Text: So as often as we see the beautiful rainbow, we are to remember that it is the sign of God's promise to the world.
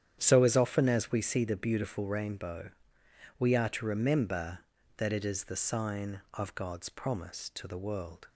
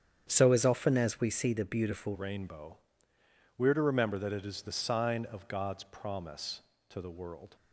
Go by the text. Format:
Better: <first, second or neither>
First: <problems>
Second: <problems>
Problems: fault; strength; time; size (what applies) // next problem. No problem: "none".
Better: first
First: starts louder than the rest; strong; until 1.2 s; 9.5 dB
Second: starts louder than the rest; strong; until 1.3 s; 8.5 dB // changes voice at "rainbow"; from 2.1 s on; 5.4 s long